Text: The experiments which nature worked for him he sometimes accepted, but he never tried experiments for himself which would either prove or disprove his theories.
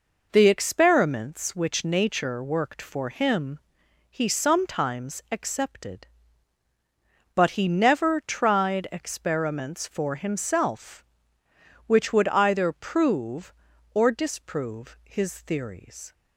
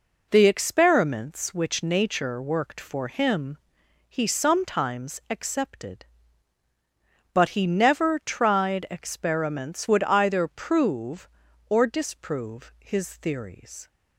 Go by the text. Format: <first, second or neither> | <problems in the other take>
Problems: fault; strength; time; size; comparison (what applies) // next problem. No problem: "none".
first | pauses between "him" and "he"; noticeable; at 3.5 s; 0.54 s long; noticeable in the first // skips "for himself which"; at 9.8 s